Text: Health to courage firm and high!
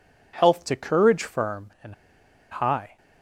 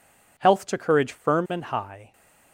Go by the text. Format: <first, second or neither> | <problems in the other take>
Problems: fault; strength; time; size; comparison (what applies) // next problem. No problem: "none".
second | pauses between "and" and "high"; noticeable; at 1.9 s; 0.56 s long